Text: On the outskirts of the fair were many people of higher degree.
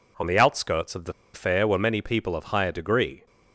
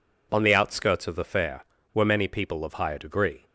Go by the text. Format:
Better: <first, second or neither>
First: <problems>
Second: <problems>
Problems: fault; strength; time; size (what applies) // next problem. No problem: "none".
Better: second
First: pauses between "the" and "fair"; slight; at 1.1 s; 0.21 s long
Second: none